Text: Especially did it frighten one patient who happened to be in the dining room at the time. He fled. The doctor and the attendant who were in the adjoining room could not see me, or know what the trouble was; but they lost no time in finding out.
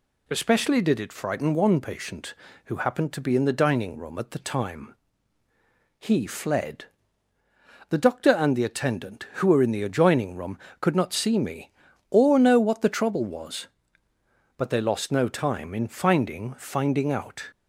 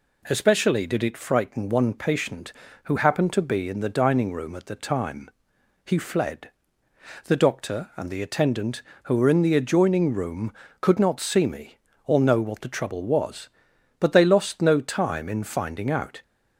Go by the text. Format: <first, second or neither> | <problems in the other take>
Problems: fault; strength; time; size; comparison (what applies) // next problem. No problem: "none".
second | says "finding" twice; at 16.5 s